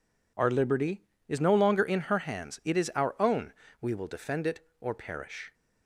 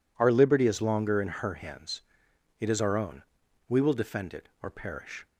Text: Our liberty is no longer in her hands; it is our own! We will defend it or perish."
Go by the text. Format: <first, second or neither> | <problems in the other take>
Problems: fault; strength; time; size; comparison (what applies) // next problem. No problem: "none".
first | skips "no"; at 0.8 s